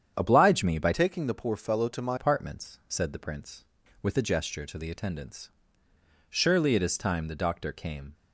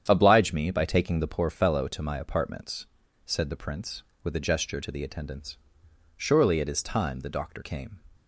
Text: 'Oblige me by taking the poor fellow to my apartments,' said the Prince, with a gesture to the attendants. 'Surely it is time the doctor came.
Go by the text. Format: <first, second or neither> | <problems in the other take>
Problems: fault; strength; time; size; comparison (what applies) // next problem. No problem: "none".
second | starts louder than the rest; strong; until 1.1 s; 8.5 dB; strong in the second // changes voice from "taking" to "my"; from 0.9 to 2.1 s; 1.2 s long